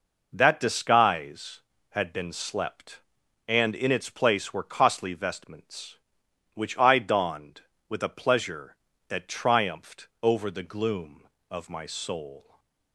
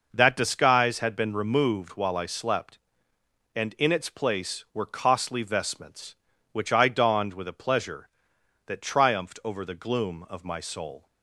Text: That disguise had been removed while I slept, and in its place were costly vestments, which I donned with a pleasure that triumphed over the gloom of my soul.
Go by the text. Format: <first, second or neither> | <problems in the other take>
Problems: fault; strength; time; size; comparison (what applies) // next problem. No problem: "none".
second | skips "removed while I"; at 2.3 s // pauses between "triumphed" and "over"; slight; at 10.0 s; 0.16 s long // stays silent after the last word; slight; from 12.4 s on; 0.5 s long